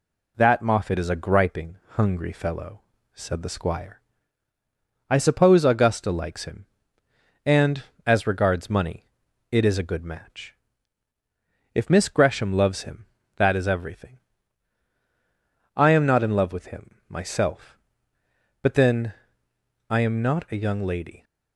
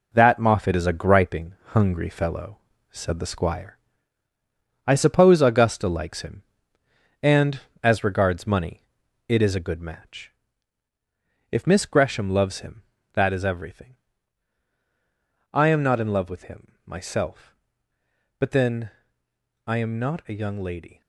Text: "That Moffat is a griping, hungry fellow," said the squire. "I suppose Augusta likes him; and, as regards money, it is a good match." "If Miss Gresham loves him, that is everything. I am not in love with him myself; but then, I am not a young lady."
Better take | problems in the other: first | gets quieter; strong; throughout; 7.5 dB

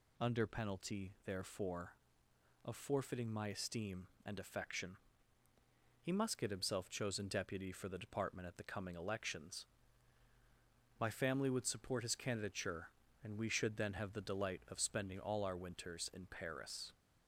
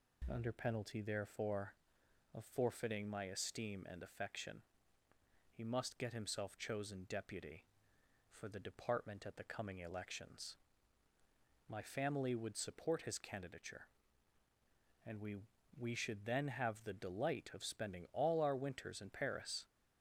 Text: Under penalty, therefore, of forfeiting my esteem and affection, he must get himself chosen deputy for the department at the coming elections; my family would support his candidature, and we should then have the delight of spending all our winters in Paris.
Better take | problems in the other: first | says "we" twice; at 15.7 s

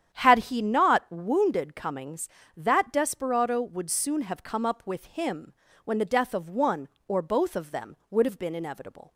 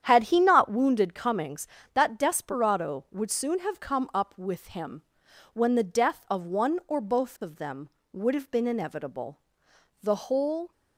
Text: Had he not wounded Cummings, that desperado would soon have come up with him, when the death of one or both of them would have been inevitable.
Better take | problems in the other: first | starts louder than the rest; strong; until 1.0 s; 9.5 dB; strong in the first // goes on to say "The whole"; noticeable; from 10.0 s on; 0.68 s long

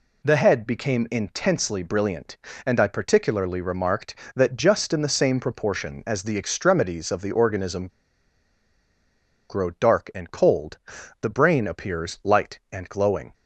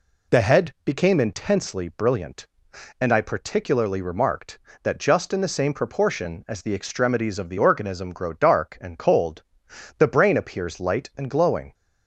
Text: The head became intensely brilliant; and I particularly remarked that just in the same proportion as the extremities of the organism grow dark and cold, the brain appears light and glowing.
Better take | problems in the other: second | pauses between "organism" and "grow"; strong; at 7.8 s; 1.6 s long

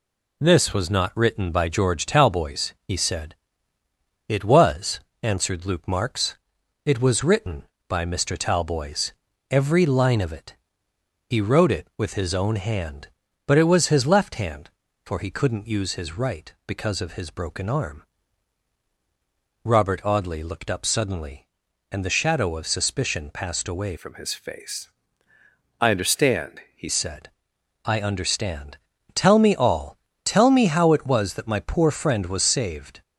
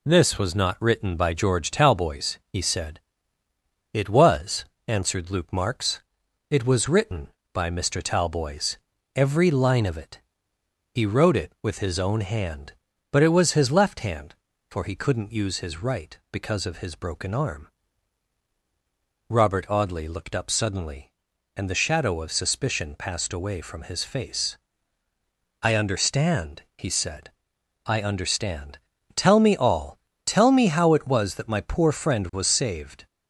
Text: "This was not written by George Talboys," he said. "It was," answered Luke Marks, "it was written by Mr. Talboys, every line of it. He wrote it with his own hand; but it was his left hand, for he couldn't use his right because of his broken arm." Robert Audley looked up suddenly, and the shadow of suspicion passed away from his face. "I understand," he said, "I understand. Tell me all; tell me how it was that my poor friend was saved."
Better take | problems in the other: second | changes voice from "from" to "he"; from 23.9 to 26.8 s; 2.9 s long

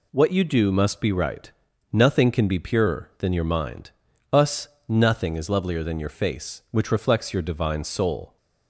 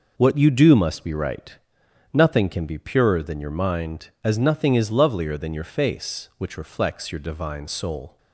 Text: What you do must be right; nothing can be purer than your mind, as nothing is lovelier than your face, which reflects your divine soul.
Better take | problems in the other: second | says "us" for "as"; at 4.3 s

